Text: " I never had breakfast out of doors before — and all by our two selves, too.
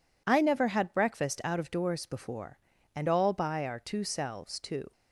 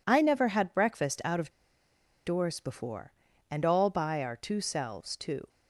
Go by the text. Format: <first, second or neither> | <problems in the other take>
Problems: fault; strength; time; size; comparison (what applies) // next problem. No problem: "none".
first | pauses between "of" and "doors"; noticeable; at 1.5 s; 0.75 s long